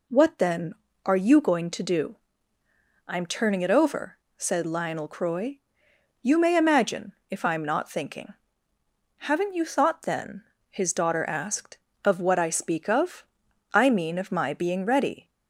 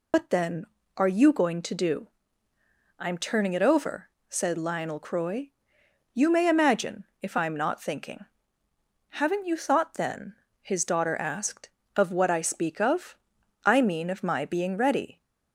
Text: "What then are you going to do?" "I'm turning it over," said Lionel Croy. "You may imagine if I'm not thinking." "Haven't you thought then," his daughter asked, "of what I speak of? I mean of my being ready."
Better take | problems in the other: first | loses the start of "What"; at 0.1 s; 130 ms // pauses between "imagine" and "if"; slight; at 7.0 s; 0.16 s long; slight in the first

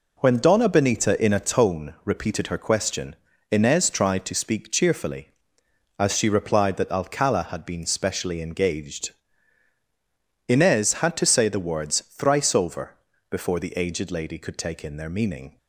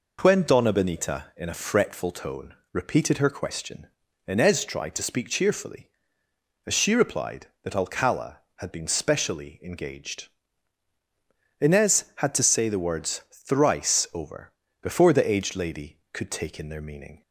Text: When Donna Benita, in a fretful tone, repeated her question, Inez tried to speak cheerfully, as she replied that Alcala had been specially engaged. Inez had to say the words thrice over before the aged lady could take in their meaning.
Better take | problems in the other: second | skips "fretful"; at 1.3 s // pauses between "over" and "before"; slight; at 12.9 s; 0.34 s long; slight in the second

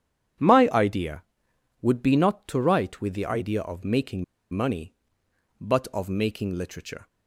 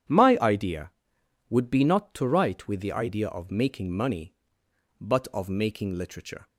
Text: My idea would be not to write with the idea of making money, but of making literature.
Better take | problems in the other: second | starts louder than the rest; strong; until 2.0 s; 9.5 dB; strong in the second // pauses between "making" and "money"; slight; at 4.2 s; 0.27 s long

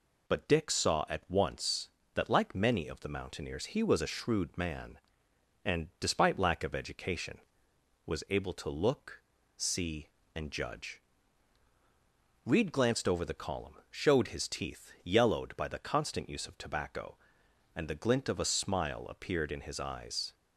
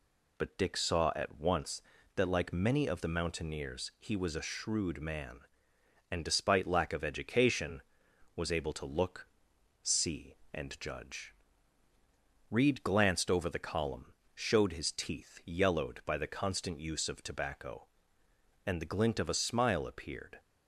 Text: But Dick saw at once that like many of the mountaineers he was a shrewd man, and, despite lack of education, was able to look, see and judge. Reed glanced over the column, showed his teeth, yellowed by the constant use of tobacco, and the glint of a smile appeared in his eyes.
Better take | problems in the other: first | stops before "in his eyes"; at 20.3 s

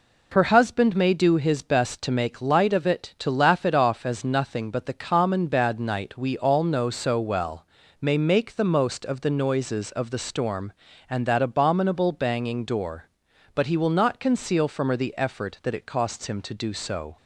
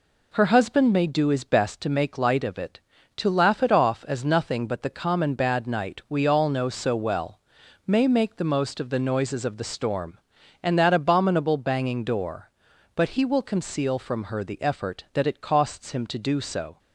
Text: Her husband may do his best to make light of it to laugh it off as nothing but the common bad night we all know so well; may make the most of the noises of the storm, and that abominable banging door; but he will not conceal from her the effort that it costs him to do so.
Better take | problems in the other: first | skips "not"; at 13.4 s

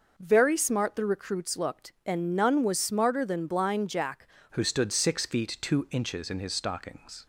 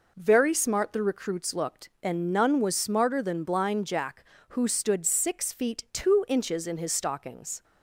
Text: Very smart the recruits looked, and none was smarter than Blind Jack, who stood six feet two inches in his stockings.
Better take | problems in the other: second | changes voice at "who"; from 4.5 s on; 2.7 s long

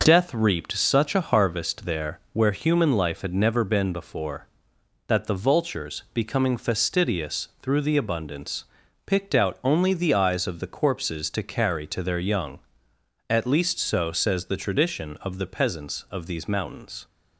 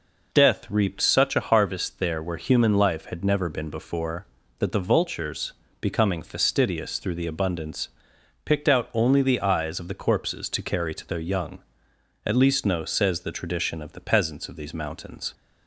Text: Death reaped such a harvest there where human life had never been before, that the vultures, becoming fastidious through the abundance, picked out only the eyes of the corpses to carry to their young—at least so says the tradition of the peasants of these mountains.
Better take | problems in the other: first | says "no" for "so"; at 12.6 s

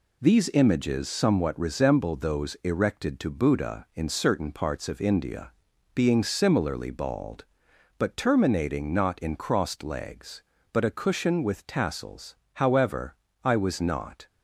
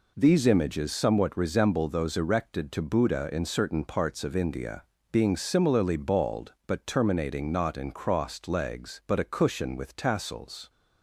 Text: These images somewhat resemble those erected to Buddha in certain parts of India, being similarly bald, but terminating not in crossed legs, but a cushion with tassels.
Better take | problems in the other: second | goes on to say "However I was not"; strong; from 12.5 s on; 1.7 s long

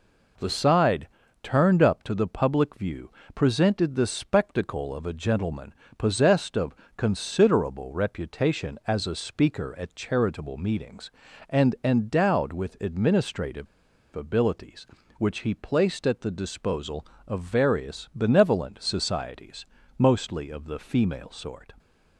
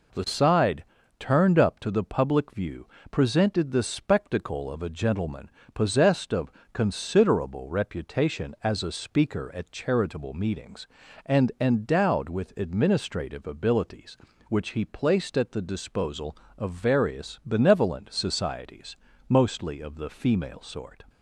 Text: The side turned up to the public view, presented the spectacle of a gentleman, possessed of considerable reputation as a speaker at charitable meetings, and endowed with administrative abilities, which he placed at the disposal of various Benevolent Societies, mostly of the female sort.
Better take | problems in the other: second | pauses between "side" and "turned"; slight; at 1.0 s; 0.34 s long; slight in the second // pauses between "of" and "considerable"; slight; at 6.7 s; 0.22 s long; slight in the second // pauses between "administrative" and "abilities"; noticeable; at 13.6 s; 0.48 s long

